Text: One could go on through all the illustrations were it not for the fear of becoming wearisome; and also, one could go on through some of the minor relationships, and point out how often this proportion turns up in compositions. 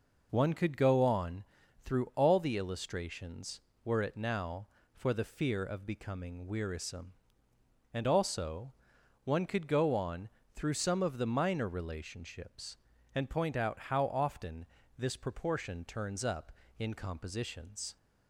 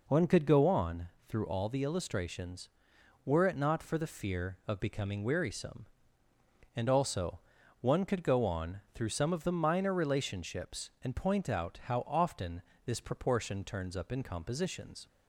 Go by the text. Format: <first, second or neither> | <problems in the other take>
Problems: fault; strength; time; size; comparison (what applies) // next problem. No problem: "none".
second | pauses between "on" and "through"; at 1.4 s; 0.42 s long; slight in the second // says "now" for "not"; at 4.1 s // pauses between "on" and "through"; slight; at 10.2 s; 0.26 s long; slight in the second // pauses between "often" and "this"; slight; at 14.6 s; 0.30 s long; slight in the second